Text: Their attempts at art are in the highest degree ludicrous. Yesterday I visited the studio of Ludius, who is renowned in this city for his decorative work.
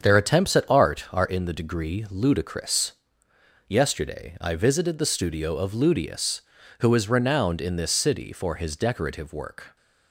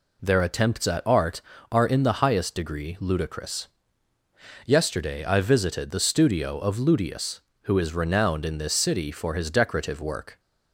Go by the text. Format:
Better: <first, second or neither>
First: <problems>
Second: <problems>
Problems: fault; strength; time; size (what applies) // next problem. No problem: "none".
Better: second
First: starts louder than the rest; strong; until 1.0 s; 7.5 dB // skips "highest"; at 1.5 s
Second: none